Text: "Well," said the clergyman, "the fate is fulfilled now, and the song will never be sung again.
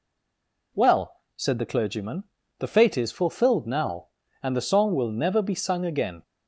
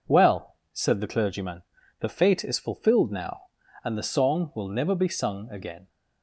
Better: second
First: stays silent before the first word; slight; until 0.7 s; 0.7 s long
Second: none

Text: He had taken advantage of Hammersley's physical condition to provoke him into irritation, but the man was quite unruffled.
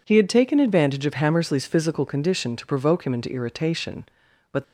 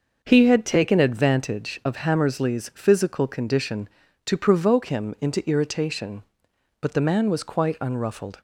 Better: second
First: stops before "the man was quite unruffled"; at 4.6 s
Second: none

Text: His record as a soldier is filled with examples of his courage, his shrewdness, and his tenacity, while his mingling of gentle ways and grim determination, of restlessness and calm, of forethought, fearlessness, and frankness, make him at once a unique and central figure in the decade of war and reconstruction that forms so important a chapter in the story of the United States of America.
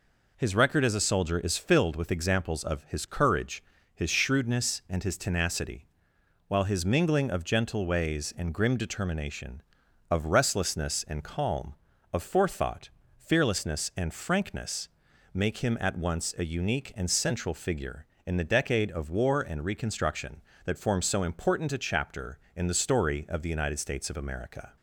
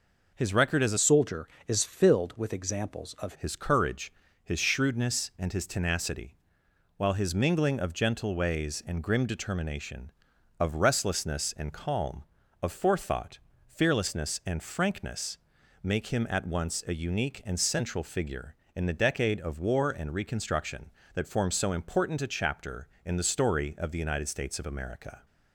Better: first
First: none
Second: changes voice from "soldier" to "of"; from 0.9 to 3.3 s; 2.4 s long

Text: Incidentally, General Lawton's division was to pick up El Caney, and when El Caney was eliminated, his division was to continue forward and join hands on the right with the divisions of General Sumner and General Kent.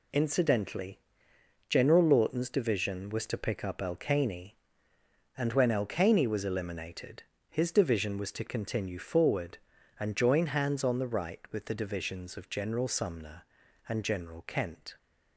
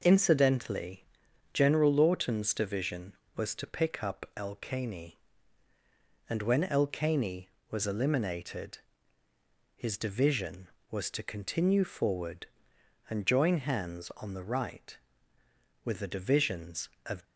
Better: first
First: none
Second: stops before "General Sumner and General Kent"; at 17.2 s

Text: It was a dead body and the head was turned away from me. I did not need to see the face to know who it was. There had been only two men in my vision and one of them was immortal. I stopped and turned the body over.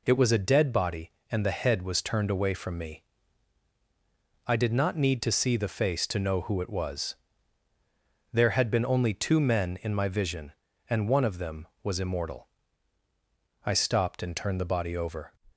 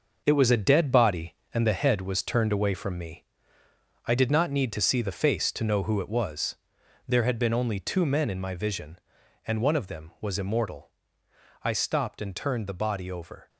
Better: first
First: none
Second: gets quieter; strong; throughout; 8.5 dB

